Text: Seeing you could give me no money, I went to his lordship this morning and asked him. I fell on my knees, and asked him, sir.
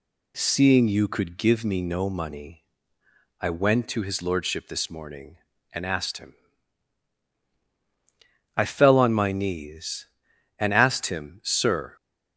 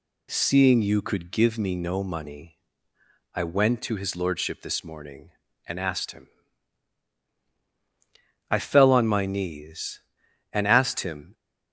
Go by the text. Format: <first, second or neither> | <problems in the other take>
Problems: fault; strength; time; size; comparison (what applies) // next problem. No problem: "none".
first | stops before "sir"; at 11.3 s